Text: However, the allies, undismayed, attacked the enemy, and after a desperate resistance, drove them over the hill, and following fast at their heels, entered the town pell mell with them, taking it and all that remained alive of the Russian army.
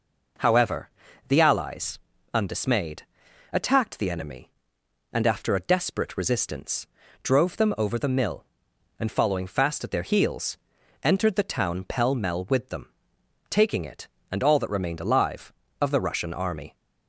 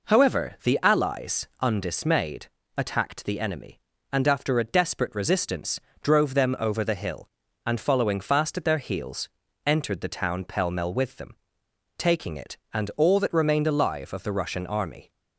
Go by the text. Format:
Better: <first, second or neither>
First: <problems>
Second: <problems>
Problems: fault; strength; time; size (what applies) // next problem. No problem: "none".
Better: second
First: says "mill" for "hill"; at 8.0 s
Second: none